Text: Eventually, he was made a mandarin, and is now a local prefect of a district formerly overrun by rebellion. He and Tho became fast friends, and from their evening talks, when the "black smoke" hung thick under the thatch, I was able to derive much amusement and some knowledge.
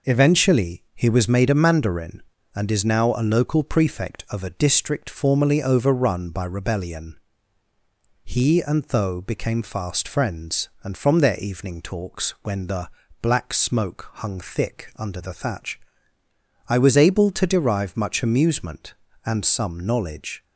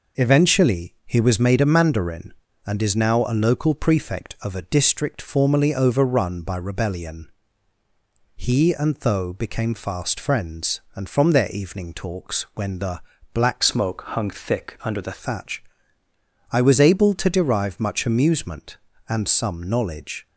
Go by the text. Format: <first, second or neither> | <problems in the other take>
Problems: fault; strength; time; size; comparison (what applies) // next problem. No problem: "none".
first | pauses between "the" and "black"; slight; at 13.0 s; 0.32 s long; slight in the first // changes voice from "smoke" to "the"; from 13.6 to 15.1 s; 1.5 s long